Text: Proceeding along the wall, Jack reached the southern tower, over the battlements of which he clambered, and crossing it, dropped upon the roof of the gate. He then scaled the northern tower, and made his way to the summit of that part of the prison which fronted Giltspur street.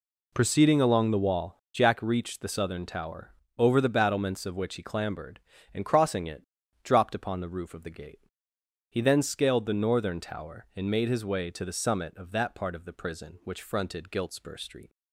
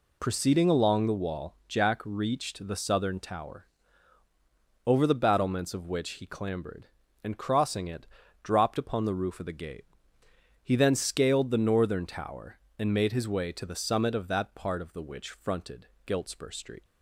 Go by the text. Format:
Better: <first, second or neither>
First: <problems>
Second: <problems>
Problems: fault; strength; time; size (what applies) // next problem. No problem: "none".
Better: first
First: none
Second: skips "prison"; at 15.0 s // pauses between "fronted" and "Giltspur"; slight; at 15.8 s; 0.20 s long